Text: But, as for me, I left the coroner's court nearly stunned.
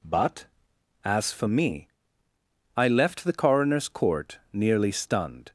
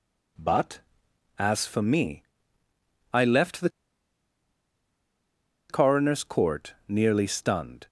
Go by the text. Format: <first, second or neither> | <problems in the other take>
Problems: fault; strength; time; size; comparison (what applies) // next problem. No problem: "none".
first | pauses between "the" and "coroner's"; strong; at 3.6 s; 2.0 s long